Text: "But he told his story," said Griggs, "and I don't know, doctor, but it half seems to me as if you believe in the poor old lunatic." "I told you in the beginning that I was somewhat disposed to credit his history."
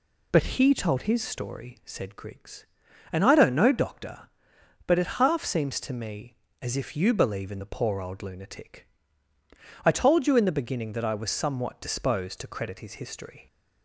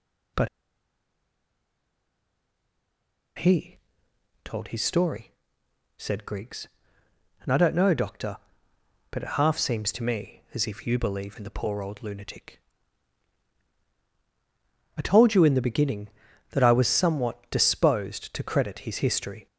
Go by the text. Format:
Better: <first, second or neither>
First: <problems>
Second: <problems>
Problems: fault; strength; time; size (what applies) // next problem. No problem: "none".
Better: first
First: none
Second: pauses between "But" and "he"; strong; at 0.4 s; 2.8 s long // pauses between "he" and "told"; noticeable; at 3.7 s; 0.64 s long